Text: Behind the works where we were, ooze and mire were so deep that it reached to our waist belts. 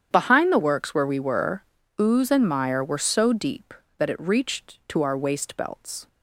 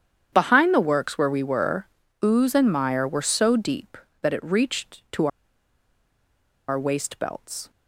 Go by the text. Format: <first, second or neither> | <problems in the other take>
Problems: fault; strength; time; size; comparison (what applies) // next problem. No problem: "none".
first | starts louder than the rest; strong; until 1.3 s; 9 dB; strong in the first // pauses between "to" and "our"; strong; at 5.2 s; 1.4 s long